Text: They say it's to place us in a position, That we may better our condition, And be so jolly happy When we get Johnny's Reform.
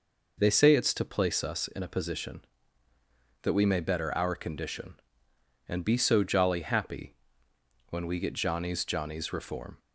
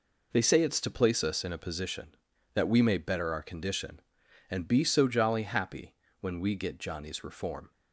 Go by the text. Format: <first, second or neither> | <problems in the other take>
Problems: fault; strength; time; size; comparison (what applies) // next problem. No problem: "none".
second | pauses between "happy" and "When"; noticeable; at 7.1 s; 0.74 s long; slight in the second // says "Johnny's" twice; at 8.8 s